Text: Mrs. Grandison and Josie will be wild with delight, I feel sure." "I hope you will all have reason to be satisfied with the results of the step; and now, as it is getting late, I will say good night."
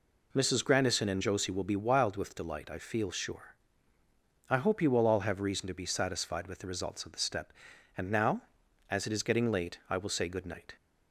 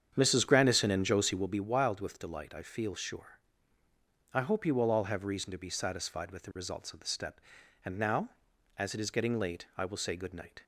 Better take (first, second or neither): first